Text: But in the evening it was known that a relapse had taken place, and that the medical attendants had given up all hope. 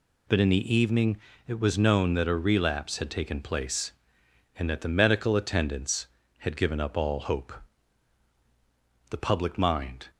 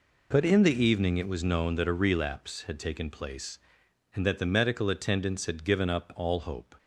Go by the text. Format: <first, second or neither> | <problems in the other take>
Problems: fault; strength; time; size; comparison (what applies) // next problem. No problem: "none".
second | pauses between "evening" and "it"; slight; at 1.1 s; 0.30 s long // goes on to say "The public mind"; noticeable; from 9.0 s on; 1.0 s long